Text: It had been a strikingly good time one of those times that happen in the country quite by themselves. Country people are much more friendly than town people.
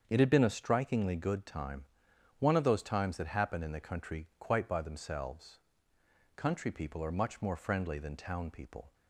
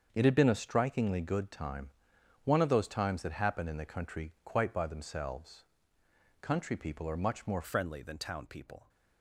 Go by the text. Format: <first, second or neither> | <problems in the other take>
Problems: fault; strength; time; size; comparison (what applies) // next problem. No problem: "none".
first | starts louder than the rest; until 1.1 s; 7 dB; strong in the first // pauses between "time" and "one"; noticeable; at 1.8 s; 0.54 s long; noticeable in the first // changes voice at "friendly"; from 7.6 s on; 1.2 s long